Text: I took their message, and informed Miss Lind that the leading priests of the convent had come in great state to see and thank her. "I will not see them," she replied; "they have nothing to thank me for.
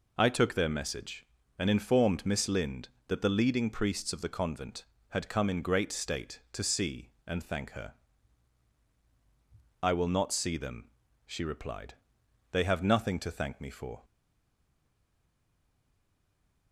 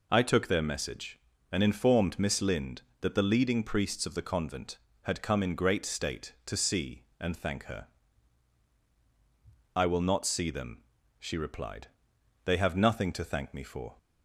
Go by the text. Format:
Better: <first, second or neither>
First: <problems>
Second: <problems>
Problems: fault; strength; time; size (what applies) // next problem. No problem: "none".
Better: second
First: stays silent after the last word; strong; from 14.0 s on; 2.7 s long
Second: none